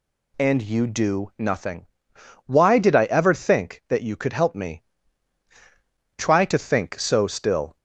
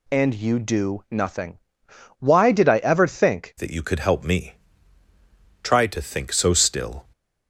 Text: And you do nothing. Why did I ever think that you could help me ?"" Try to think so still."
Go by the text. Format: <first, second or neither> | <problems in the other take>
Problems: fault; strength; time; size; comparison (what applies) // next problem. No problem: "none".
first | changes voice at "that"; from 3.5 s on; 3.5 s long